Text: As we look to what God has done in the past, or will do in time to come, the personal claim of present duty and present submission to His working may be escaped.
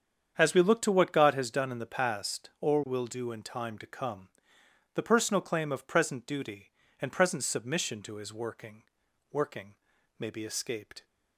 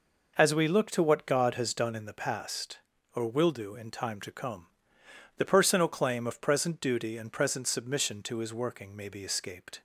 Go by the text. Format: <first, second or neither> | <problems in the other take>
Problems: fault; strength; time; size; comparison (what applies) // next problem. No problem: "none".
second | starts louder than the rest; strong; until 1.3 s; 8 dB // says "working" twice; at 9.3 s